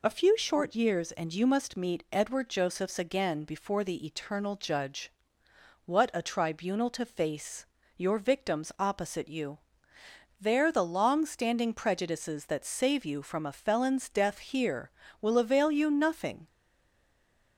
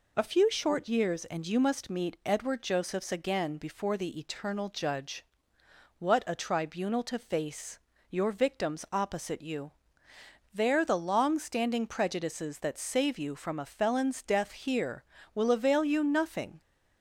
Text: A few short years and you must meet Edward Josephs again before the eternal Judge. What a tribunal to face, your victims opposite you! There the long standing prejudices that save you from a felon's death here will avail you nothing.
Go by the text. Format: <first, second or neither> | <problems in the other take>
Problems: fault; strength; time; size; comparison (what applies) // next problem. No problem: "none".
second | stays silent after the last word; from 16.4 s on; 1.1 s long